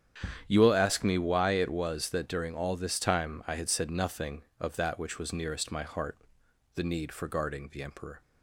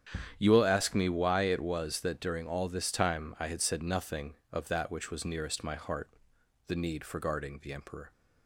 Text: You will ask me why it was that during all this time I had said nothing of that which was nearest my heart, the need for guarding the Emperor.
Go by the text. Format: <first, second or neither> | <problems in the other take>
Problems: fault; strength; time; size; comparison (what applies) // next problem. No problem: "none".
neither | starts louder than the rest; strong; the same in both